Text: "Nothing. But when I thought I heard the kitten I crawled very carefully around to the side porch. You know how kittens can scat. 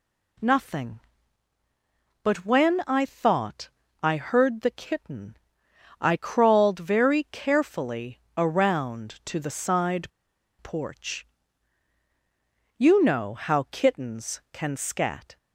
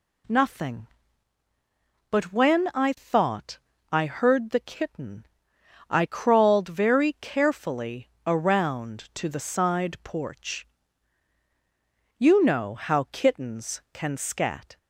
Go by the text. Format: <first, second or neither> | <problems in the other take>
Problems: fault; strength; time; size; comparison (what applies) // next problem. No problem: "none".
second | pauses between "thought" and "I"; slight; at 3.7 s; 0.32 s long; slight in the second // pauses between "kitten" and "I"; noticeable; at 5.3 s; 0.64 s long; noticeable in the second // pauses between "carefully" and "around"; slight; at 8.2 s; 0.16 s long; slight in the second // pauses between "side" and "porch"; noticeable; at 10.1 s; 0.50 s long